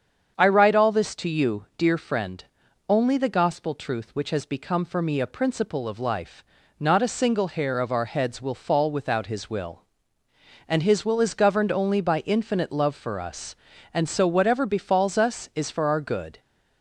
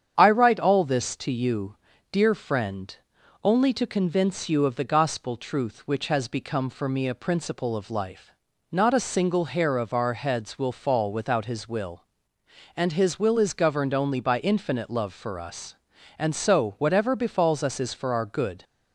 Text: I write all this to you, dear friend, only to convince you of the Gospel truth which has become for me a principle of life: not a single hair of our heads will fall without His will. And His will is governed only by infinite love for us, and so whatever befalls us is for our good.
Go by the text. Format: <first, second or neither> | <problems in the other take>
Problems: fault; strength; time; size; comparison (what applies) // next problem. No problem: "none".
second | starts louder than the rest; strong; until 1.3 s; 7.5 dB; strong in the second // skips "to convince you of"; at 3.1 s